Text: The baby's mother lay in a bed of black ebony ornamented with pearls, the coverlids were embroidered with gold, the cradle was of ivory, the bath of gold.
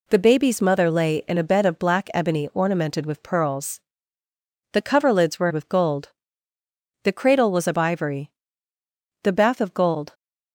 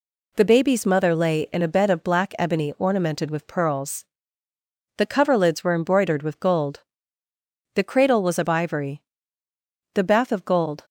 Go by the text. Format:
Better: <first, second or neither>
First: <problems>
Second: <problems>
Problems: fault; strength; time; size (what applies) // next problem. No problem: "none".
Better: second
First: skips "embroidered"; at 5.5 s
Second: none